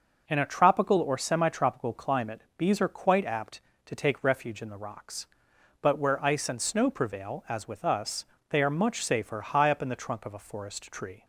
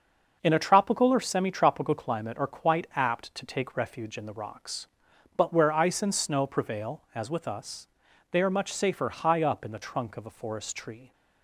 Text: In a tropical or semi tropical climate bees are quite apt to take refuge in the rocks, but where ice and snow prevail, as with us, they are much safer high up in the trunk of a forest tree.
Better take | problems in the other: first | starts louder than the rest; until 1.4 s; 6 dB; noticeable in the first // skips "bees"; at 2.3 s

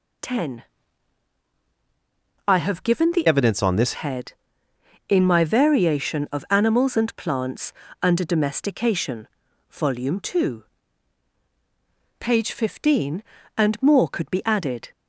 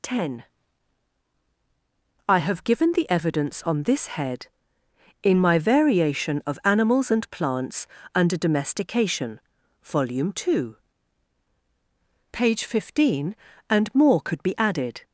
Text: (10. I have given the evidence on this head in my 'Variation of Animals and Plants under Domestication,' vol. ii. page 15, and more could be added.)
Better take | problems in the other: second | changes voice from "evidence" to "this"; from 3.2 to 3.9 s; 0.7 s long // pauses between "Plants" and "under"; slight; at 7.7 s; 0.30 s long; slight in the second

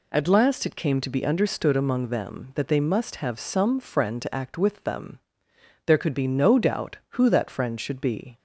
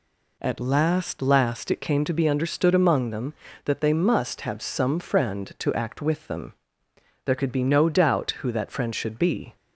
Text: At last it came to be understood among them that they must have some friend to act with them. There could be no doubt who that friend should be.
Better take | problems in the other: first | says "last" twice; at 1.1 s

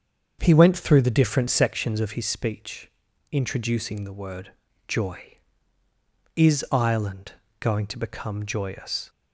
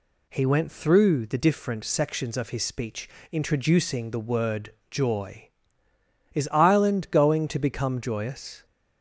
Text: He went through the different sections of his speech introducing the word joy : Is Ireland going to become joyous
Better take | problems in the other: second | starts louder than the rest; until 1.8 s; 7 dB // pauses between "speech" and "introducing"; at 2.8 s; 0.42 s long; slight in the second // pauses between "word" and "joy"; slight; at 4.5 s; 0.36 s long; slight in the second // pauses between "Ireland" and "going"; slight; at 7.3 s; 0.26 s long

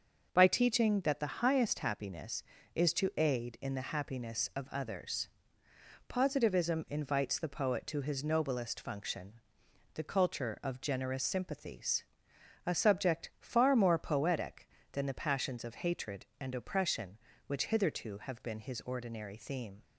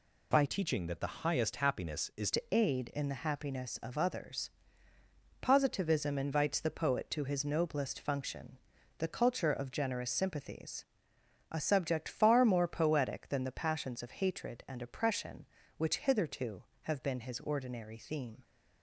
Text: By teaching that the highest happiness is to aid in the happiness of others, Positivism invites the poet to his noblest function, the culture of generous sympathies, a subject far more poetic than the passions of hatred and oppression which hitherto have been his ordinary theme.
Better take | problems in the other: first | changes voice from "teaching" to "is"; from 0.4 to 2.2 s; 1.8 s long

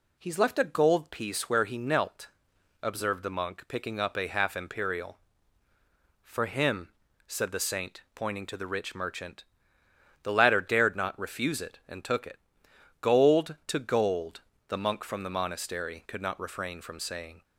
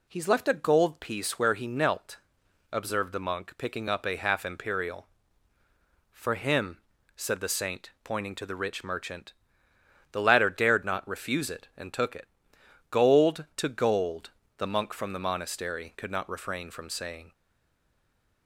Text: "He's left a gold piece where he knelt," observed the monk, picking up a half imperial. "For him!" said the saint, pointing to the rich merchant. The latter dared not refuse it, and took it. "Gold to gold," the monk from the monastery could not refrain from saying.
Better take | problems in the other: first | stays silent after the last word; from 17.3 s on; 1.1 s long

